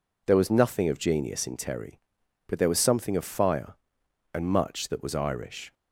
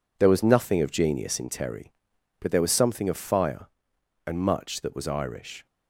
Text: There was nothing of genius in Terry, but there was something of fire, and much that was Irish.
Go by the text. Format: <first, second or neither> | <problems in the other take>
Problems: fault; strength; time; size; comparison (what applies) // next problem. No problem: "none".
first | gets quieter; strong; throughout; 9 dB